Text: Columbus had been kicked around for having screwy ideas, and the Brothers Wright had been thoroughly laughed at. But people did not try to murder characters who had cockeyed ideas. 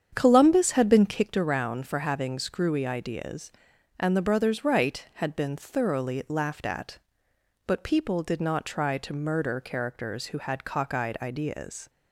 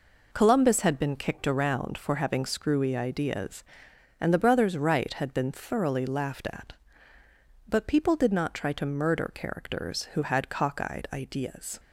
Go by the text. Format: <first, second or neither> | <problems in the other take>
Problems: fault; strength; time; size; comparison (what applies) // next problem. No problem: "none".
second | starts louder than the rest; strong; until 1.4 s; 8 dB